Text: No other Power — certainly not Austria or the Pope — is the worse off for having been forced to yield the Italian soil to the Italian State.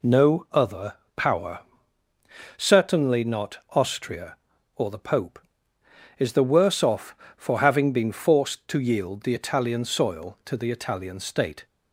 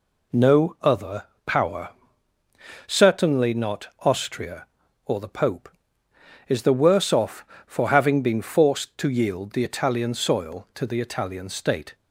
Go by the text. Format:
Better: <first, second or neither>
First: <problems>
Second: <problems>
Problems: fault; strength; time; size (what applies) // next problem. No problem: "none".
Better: neither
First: pauses between "other" and "Power"; slight; at 0.9 s; 0.22 s long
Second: pauses between "other" and "Power"; slight; at 1.2 s; 0.22 s long